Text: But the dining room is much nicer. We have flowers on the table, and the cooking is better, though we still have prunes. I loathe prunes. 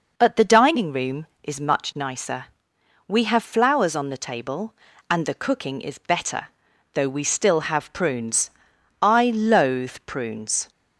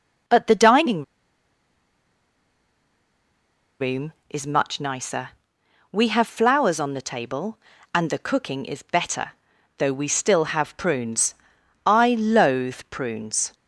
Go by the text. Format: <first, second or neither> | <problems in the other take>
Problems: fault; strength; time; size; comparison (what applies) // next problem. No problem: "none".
first | pauses between "dining" and "room"; strong; at 1.0 s; 2.7 s long